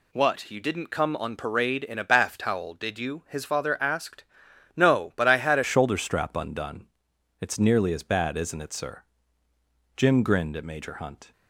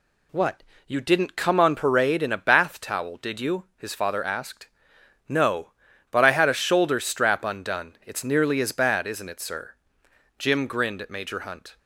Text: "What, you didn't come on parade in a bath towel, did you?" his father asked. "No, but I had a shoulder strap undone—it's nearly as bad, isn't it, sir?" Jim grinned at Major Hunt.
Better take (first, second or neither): second